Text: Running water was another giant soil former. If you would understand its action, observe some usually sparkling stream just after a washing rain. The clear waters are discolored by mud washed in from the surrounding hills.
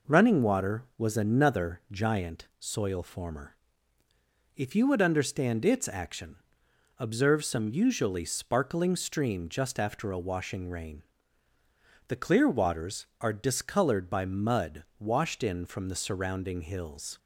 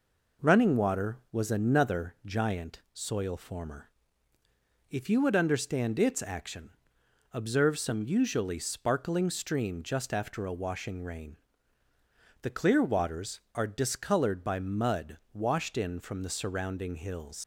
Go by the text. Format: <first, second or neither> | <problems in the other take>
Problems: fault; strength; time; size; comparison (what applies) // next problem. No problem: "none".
first | pauses between "mud" and "washed"; slight; at 15.1 s; 0.16 s long; slight in the first // leaves "hills" unfinished; at 17.4 s; 80 ms